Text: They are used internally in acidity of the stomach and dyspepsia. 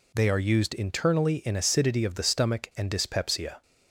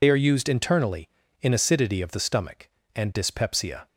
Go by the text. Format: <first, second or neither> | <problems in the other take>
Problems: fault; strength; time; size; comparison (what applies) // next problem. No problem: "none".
first | loses the start of "They"; at 0.0 s; 50 ms